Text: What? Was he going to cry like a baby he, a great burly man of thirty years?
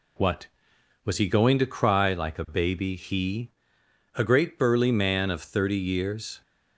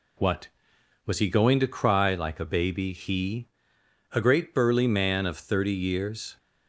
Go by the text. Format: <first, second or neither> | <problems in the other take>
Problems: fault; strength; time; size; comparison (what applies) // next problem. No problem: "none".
neither | none